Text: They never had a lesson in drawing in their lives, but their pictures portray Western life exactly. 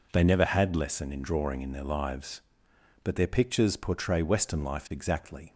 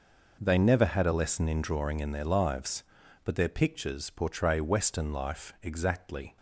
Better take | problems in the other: second | skips "a"; at 0.7 s

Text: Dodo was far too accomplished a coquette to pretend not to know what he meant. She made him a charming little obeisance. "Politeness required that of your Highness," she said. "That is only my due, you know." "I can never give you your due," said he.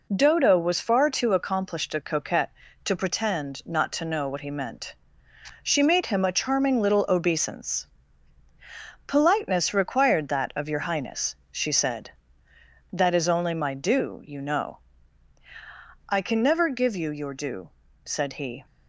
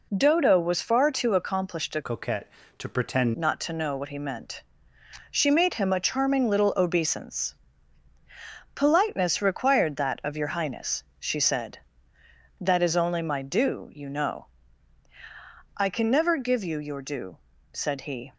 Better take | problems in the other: first | changes voice from "coquette" to "pretend"; from 2.0 to 3.3 s; 1.3 s long

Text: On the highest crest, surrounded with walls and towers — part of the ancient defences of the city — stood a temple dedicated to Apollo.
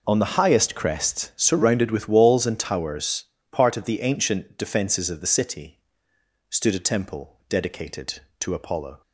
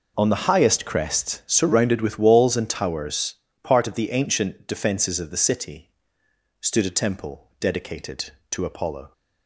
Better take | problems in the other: neither | none

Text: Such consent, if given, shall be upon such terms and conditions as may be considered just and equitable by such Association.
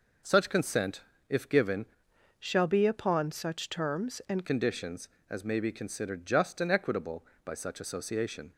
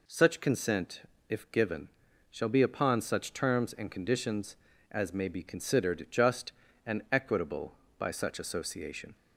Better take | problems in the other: second | changes voice from "shall" to "and"; from 2.4 to 4.4 s; 2.0 s long

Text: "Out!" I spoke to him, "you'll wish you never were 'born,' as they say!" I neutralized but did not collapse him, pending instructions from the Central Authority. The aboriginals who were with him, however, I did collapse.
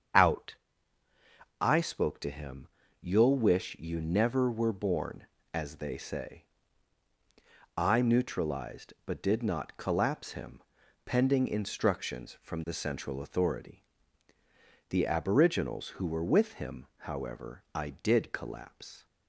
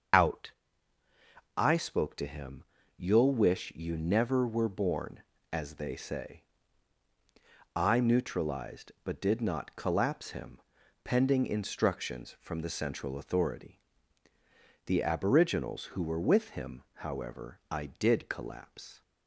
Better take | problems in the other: first | loses the start of "Out"; at 0.1 s; 35 ms // starts louder than the rest; until 2.2 s; 6.5 dB; strong in the first

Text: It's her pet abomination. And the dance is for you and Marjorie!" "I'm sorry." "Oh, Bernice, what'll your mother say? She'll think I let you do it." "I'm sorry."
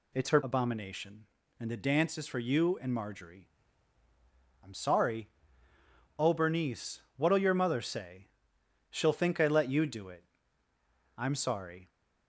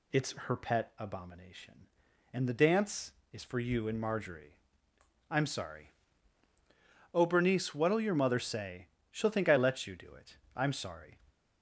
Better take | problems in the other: second | skips "pet"; at 0.4 s

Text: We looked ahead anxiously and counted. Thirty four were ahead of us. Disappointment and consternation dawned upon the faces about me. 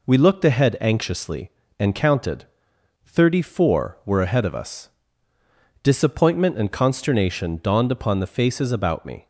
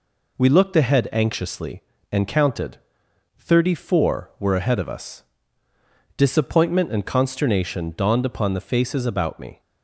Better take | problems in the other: neither | none

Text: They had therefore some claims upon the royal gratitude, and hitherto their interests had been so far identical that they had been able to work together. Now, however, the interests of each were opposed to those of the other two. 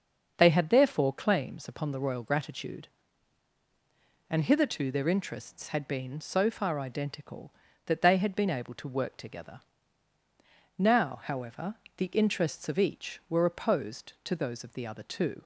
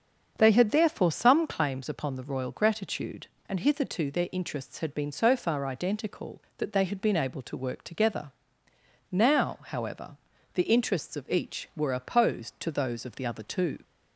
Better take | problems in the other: second | starts louder than the rest; until 1.3 s; 6.5 dB; also in the second // skips "some"; at 1.1 s

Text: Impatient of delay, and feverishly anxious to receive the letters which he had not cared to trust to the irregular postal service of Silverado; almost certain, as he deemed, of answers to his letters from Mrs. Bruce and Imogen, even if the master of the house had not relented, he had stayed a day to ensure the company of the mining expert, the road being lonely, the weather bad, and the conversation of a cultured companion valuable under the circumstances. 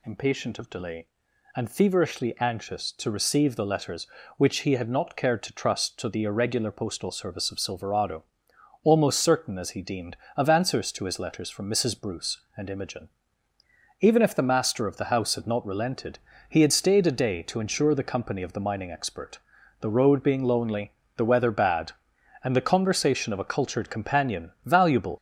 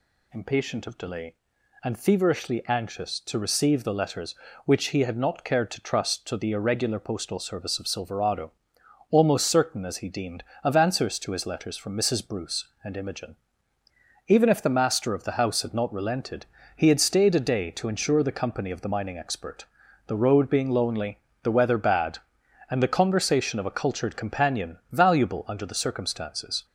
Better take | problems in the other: second | stops before "under the circumstances"; at 25.1 s

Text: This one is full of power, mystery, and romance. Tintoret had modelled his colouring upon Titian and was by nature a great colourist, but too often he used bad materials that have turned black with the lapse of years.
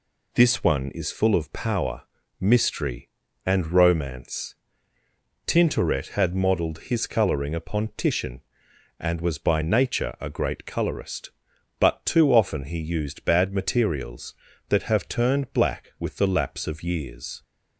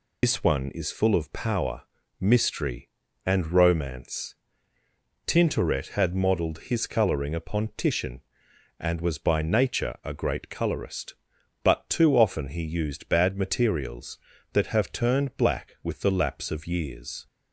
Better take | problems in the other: first | loses the start of "This"; at 0.2 s; 95 ms

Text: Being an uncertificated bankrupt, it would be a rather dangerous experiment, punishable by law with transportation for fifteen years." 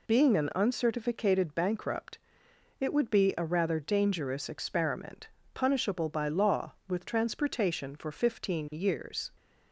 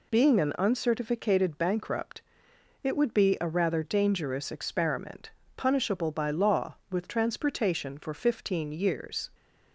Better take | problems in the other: neither | none

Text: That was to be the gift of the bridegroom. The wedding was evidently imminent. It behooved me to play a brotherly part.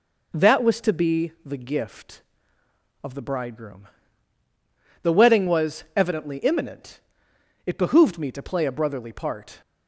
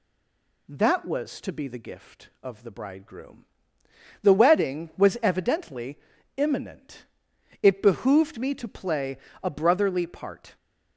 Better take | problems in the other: first | stays silent before the first word; slight; until 0.6 s; 0.6 s long // pauses between "evidently" and "imminent"; at 5.9 s; 0.38 s long // pauses between "play" and "a"; slight; at 9.1 s; 0.24 s long

